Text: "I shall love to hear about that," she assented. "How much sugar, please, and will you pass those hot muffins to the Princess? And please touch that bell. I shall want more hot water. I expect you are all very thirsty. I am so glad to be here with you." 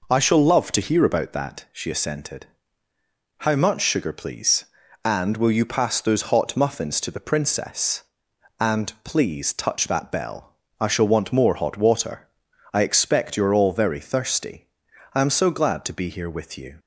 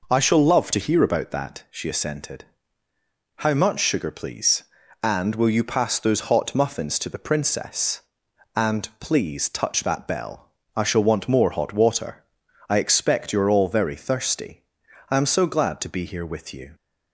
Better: neither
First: none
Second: none

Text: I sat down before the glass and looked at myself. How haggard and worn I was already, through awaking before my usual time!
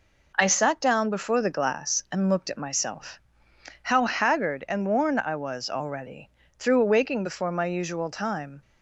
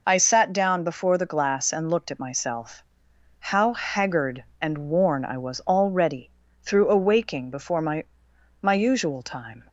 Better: first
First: none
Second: says "my" twice; at 8.5 s

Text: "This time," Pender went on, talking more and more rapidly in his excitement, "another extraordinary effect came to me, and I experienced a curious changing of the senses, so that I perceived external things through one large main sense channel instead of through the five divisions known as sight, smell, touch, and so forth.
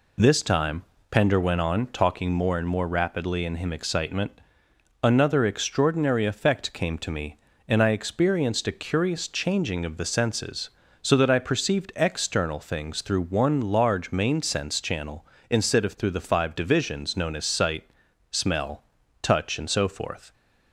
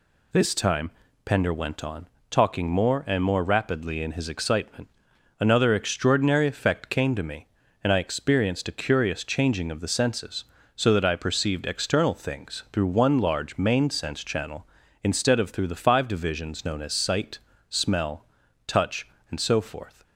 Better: second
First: says "him" for "his"; at 3.5 s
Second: none

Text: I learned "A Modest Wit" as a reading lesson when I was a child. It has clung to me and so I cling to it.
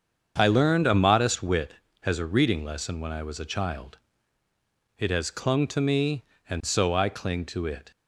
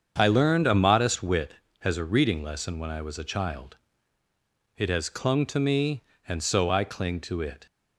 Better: neither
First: starts louder than the rest; strong; until 1.3 s; 7 dB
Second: starts louder than the rest; strong; until 1.1 s; 7 dB

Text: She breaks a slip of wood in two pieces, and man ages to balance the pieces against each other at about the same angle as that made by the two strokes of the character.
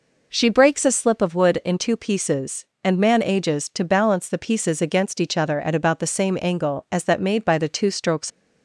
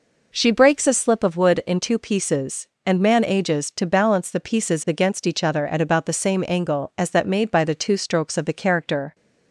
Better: second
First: stops before "of the character"; at 8.3 s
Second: none

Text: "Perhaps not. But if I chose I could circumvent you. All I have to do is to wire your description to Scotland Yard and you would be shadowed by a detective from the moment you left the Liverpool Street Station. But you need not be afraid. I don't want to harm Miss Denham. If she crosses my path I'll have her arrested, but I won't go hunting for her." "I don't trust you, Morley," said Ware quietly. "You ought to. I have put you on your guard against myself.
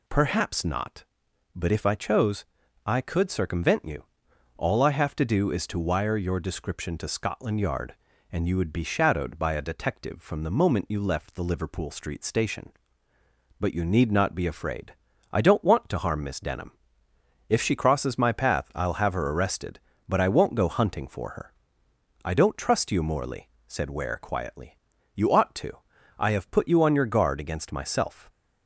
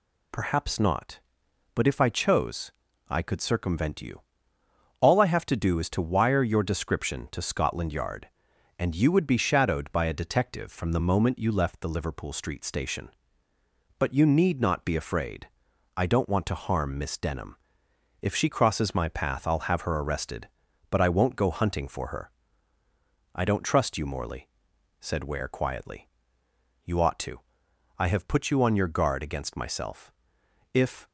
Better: first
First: pauses between "chose" and "I"; at 2.4 s; 0.44 s long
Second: pauses between "chose" and "I"; at 2.7 s; 0.40 s long // goes on to say "If"; slight; from 30.7 s on; 0.34 s long

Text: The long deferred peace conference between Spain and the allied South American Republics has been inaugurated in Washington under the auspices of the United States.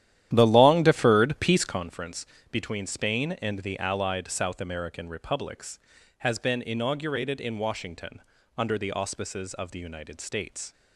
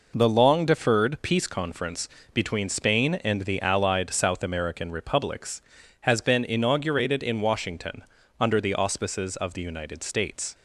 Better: second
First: starts louder than the rest; strong; until 1.9 s; 11.5 dB // pauses between "conference" and "between"; slight; at 2.2 s; 0.26 s long // pauses between "Washington" and "under"; slight; at 8.2 s; 0.34 s long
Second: pauses between "conference" and "between"; slight; at 2.0 s; 0.26 s long // pauses between "Washington" and "under"; slight; at 8.0 s; 0.34 s long

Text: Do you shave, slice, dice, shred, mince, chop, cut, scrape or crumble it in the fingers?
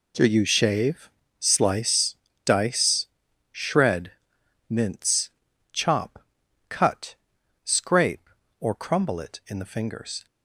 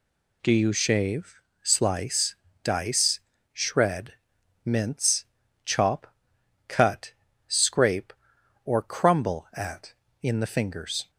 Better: first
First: none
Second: says "at" for "it"; at 9.5 s

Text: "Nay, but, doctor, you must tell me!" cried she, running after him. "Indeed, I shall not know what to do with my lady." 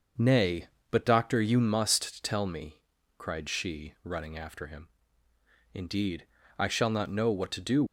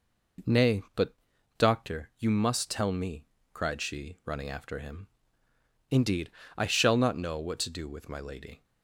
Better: second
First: starts louder than the rest; until 1.4 s; 6 dB // stops before "with my lady"; at 7.8 s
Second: none

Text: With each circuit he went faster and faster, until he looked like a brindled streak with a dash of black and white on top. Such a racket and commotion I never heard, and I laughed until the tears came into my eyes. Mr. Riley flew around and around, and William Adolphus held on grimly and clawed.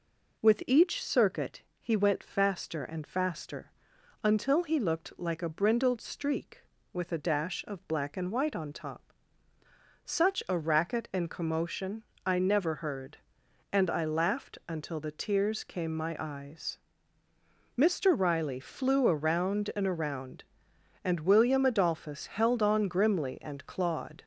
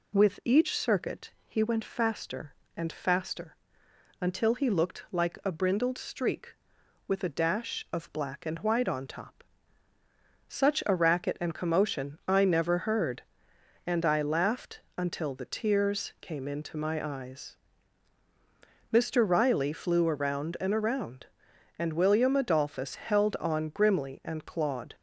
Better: second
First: pauses between "circuit" and "he"; slight; at 1.6 s; 0.16 s long // pauses between "commotion" and "I"; slight; at 12.0 s; 0.20 s long // skips "into"; at 15.9 s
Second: pauses between "circuit" and "he"; slight; at 1.3 s; 0.16 s long

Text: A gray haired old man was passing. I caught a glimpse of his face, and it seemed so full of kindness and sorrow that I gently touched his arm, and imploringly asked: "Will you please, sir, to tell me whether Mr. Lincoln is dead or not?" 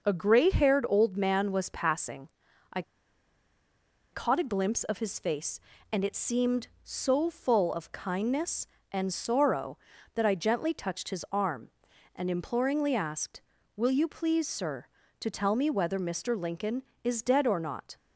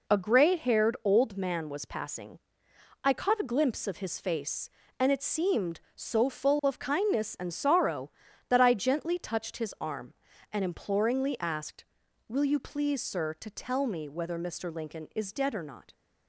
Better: second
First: pauses between "I" and "caught"; strong; at 2.8 s; 1.3 s long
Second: none

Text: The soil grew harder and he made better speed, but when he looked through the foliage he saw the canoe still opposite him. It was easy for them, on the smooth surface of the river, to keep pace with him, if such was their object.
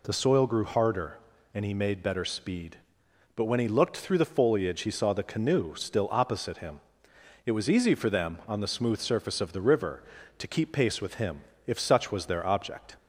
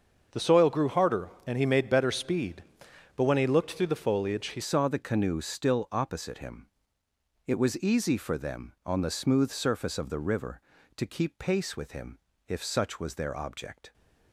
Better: first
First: none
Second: starts louder than the rest; until 1.4 s; 6.5 dB // changes voice at "saw"; from 4.6 s on; 9.3 s long

